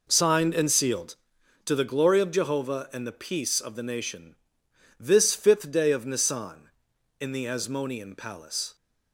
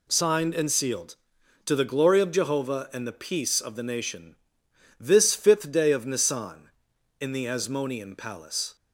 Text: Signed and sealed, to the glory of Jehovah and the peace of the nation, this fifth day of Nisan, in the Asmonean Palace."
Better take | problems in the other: second | starts louder than the rest; noticeable; until 1.3 s; 4.5 dB

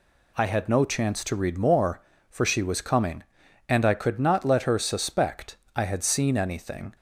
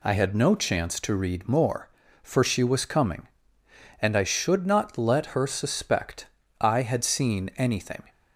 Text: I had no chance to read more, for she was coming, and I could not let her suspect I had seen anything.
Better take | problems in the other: first | says "should" for "could"; at 4.2 s // pauses between "suspect" and "I"; slight; at 6.2 s; 0.32 s long; slight in the first

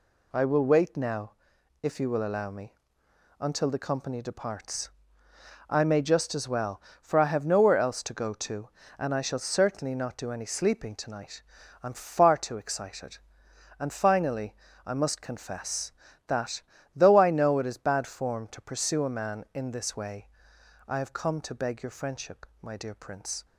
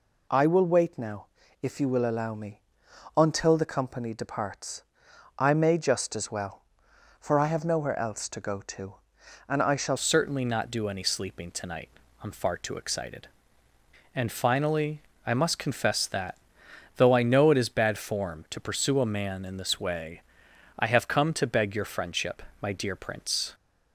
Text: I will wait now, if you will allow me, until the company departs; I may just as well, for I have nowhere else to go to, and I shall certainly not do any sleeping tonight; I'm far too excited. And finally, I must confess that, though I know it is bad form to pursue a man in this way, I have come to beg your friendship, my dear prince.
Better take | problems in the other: first | changes voice at "certainly"; from 9.9 s on; 13.6 s long

